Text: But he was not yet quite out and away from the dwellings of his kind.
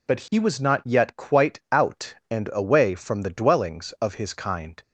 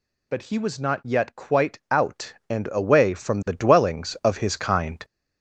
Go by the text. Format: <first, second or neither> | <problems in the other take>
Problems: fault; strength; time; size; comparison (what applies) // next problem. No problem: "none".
first | gets louder; throughout; 6 dB